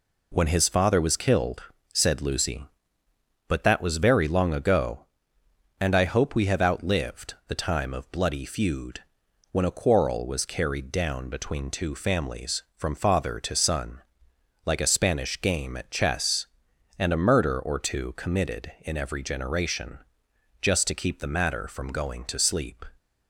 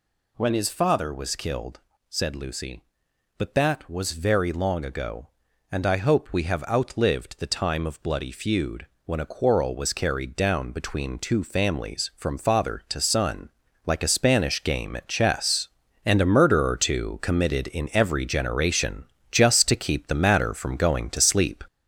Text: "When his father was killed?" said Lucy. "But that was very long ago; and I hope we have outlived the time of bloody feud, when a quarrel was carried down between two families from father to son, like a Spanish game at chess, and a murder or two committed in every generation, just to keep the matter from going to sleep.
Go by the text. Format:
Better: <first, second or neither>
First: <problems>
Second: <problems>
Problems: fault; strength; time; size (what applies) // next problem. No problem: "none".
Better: first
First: none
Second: gets louder; throughout; 6 dB